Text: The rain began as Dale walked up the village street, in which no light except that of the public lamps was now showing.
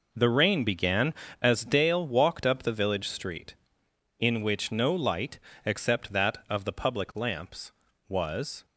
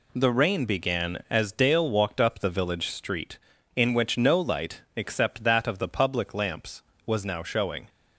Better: second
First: pauses between "light" and "except"; slight; at 5.3 s; 0.26 s long // stops before "now showing"; at 8.6 s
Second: none

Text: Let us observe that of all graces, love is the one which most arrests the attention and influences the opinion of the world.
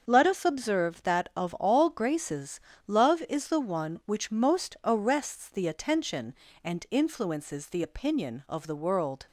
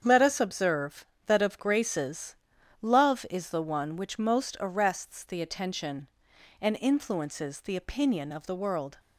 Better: first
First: starts louder than the rest; until 1.0 s; 6.5 dB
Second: starts louder than the rest; strong; until 1.0 s; 7.5 dB // skips "all"; at 1.5 s

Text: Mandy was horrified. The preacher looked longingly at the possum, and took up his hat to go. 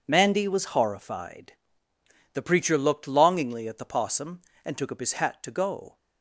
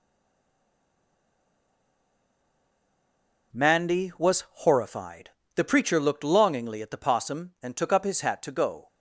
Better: first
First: none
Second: stays silent before the first word; strong; until 3.5 s; 3.5 s long // pauses between "was" and "horrified"; slight; at 4.4 s; 0.18 s long

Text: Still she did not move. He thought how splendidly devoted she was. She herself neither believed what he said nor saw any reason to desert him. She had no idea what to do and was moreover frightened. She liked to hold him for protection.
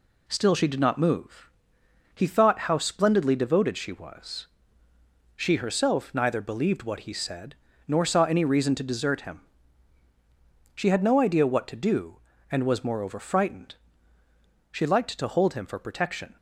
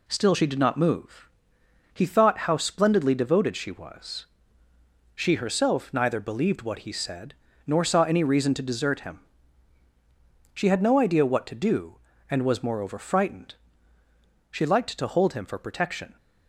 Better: neither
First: pauses between "said" and "nor"; slight; at 7.5 s; 0.34 s long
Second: pauses between "said" and "nor"; slight; at 7.3 s; 0.34 s long

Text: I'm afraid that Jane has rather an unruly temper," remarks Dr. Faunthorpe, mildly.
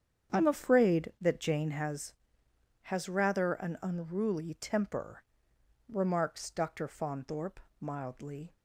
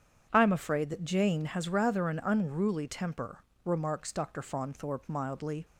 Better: second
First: starts louder than the rest; strong; until 1.4 s; 8 dB // says "has" twice; at 2.8 s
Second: starts louder than the rest; strong; until 1.3 s; 8 dB

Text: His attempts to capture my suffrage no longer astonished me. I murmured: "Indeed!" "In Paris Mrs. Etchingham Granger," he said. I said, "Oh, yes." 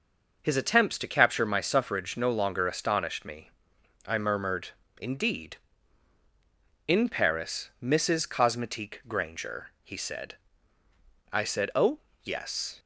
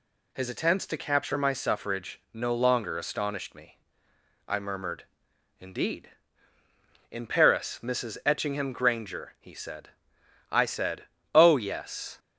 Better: second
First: says "Cosmetique" for "Etchingham"; at 8.2 s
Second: none

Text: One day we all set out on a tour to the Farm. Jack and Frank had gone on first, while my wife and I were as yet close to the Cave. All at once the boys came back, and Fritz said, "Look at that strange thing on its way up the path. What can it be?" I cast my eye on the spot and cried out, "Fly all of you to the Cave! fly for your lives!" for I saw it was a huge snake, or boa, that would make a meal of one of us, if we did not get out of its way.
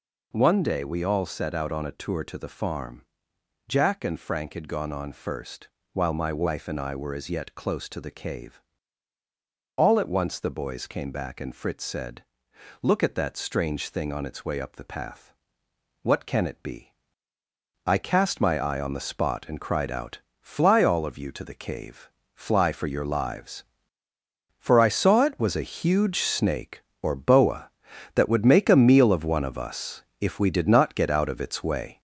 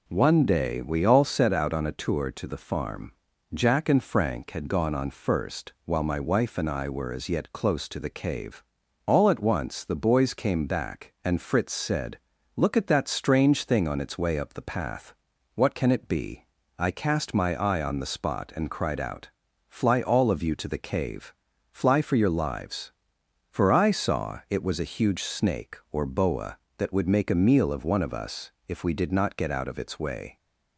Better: second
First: gets louder; noticeable; throughout; 4 dB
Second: none

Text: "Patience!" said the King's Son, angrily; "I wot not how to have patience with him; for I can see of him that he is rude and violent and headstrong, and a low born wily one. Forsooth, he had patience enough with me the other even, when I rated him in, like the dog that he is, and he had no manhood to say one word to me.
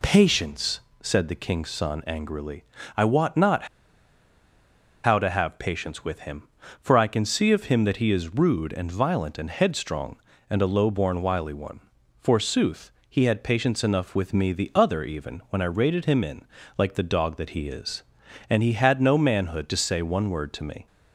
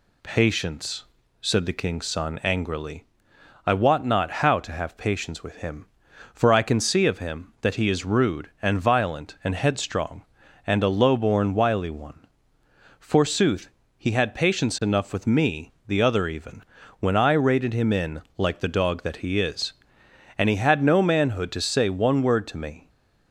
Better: second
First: pauses between "not" and "how"; strong; at 3.6 s; 1.3 s long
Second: none

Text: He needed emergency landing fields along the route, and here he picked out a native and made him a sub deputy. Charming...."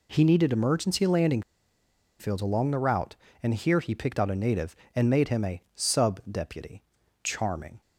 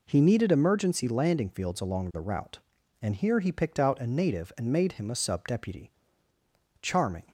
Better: second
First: pauses between "landing" and "fields"; noticeable; at 1.4 s; 0.78 s long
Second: none

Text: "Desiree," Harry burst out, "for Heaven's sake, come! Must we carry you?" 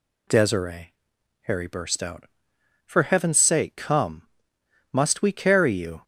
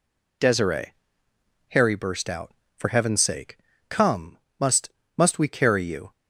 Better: first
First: none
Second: says "Must" twice; at 5.1 s

